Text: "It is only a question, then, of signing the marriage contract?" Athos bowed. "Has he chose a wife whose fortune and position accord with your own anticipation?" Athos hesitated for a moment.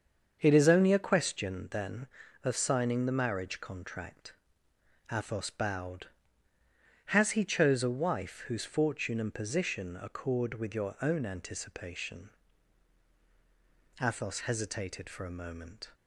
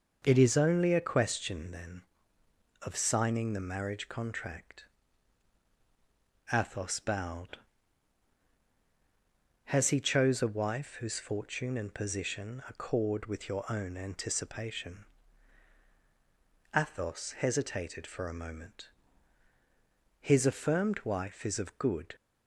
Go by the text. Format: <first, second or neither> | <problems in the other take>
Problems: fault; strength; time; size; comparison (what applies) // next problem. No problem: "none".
first | starts louder than the rest; noticeable; until 1.2 s; 6 dB; also in the first // goes on to say "His affirmed wife is of good"; strong; from 20.2 s on; 1.9 s long